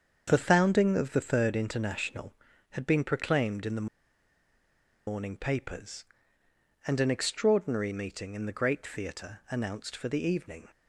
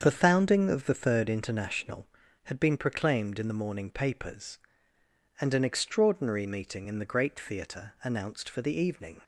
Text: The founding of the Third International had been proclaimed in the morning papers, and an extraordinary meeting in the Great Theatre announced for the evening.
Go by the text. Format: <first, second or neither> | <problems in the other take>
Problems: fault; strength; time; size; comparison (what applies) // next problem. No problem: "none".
second | starts louder than the rest; strong; until 1.2 s; 7 dB; strong in the second // pauses between "the" and "morning"; at 3.8 s; 1.2 s long